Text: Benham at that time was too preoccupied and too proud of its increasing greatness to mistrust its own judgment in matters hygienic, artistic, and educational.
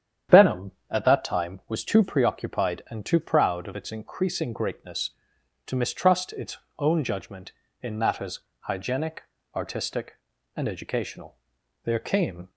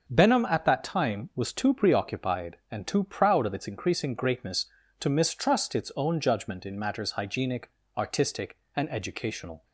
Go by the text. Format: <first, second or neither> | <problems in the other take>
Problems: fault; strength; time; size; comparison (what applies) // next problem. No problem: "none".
second | starts louder than the rest; strong; until 1.4 s; 9.5 dB // pauses between "its" and "own"; slight; at 6.5 s; 0.20 s long // pauses between "matters" and "hygienic"; slight; at 8.4 s; 0.20 s long // goes on to say "There came"; noticeable; from 11.8 s on; 0.64 s long